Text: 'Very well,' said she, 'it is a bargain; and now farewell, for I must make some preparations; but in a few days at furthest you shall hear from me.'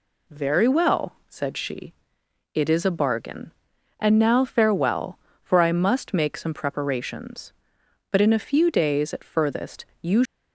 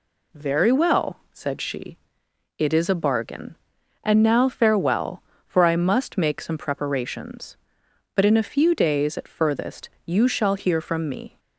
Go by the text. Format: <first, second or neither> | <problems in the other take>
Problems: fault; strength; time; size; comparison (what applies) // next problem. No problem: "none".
second | pauses between "furthest" and "you"; slight; at 9.8 s; 0.16 s long; slight in the second // stops before "shall hear from me"; at 10.2 s